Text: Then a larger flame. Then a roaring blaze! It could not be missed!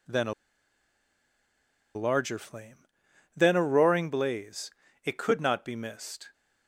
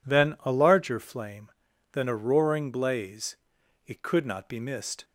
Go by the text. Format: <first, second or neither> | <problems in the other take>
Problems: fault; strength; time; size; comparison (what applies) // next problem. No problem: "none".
second | pauses between "a" and "larger"; strong; at 0.3 s; 1.6 s long